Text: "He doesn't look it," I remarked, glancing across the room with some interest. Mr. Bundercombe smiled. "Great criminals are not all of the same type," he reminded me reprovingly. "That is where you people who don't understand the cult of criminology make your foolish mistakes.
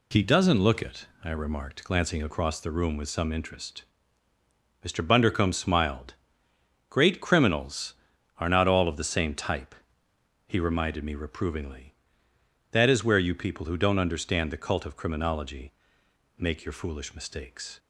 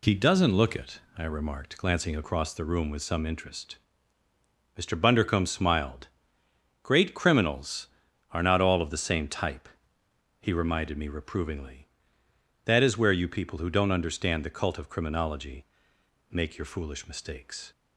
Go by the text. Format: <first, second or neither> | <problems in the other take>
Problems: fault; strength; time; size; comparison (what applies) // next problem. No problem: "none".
neither | pauses between "criminology" and "make"; noticeable; the same in both